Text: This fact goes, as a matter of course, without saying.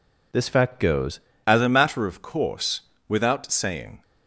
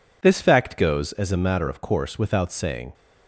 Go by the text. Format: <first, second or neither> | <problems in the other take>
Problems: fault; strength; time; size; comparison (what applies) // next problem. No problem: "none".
second | changes voice at "as"; from 1.4 s on; 2.6 s long